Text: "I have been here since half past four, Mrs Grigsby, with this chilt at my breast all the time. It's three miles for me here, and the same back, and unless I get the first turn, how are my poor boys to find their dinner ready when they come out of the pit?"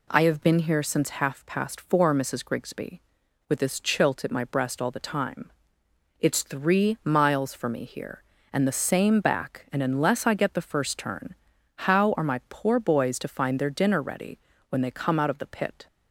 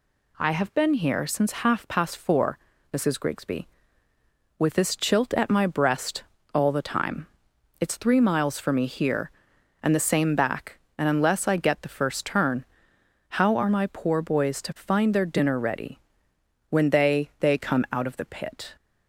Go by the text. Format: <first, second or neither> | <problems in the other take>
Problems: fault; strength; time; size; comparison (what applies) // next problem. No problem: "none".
first | pauses between "breast" and "all"; slight; at 6.2 s; 0.30 s long // pauses between "ready" and "when"; noticeable; at 15.9 s; 0.70 s long; slight in the first // says "they" twice; at 17.3 s